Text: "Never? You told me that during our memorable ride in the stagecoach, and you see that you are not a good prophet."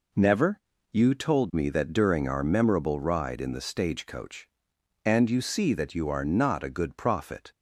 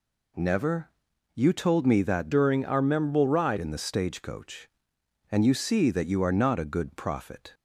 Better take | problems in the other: first | changes voice from "during" to "ride"; from 2.3 to 3.5 s; 1.2 s long

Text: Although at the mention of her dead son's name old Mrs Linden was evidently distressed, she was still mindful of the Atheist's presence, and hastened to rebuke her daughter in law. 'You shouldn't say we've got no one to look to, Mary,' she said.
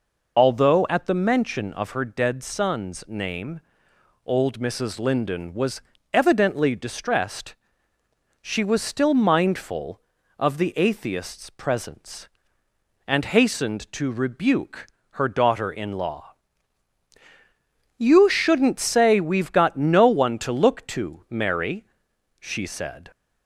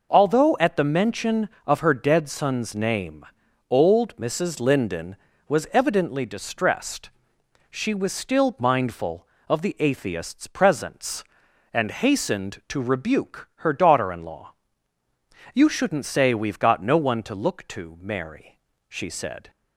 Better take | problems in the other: second | loses the start of "Although"; at 0.3 s; 40 ms // pauses between "name" and "old"; noticeable; at 3.6 s; 0.66 s long; noticeable in the second // pauses between "was" and "evidently"; slight; at 5.8 s; 0.32 s long // pauses between "rebuke" and "her"; slight; at 14.8 s; 0.26 s long

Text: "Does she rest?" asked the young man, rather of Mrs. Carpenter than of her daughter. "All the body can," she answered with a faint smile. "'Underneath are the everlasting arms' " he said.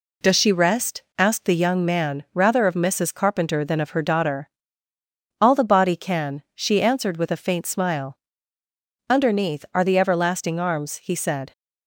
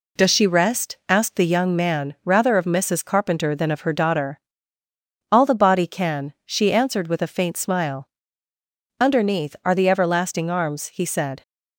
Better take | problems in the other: neither | none

